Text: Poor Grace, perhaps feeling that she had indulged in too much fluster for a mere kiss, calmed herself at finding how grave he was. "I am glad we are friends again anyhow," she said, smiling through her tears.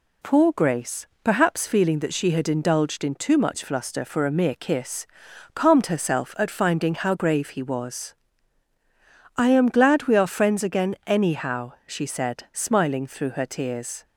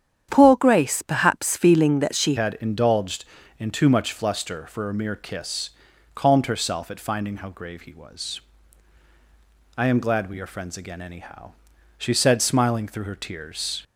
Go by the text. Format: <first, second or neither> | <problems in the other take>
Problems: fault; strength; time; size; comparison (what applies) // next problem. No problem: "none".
first | starts louder than the rest; strong; until 1.3 s; 9 dB // changes voice at "had"; from 2.3 s on; 11.5 s long